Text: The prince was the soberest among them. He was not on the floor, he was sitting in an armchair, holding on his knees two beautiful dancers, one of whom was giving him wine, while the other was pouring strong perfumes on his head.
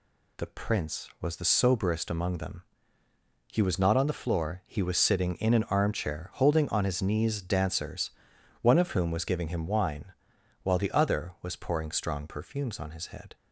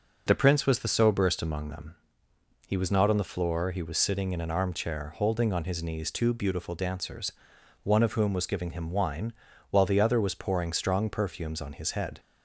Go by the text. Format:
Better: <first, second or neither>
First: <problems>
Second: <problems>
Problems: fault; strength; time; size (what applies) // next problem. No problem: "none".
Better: second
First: skips "two beautiful"; at 7.3 s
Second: none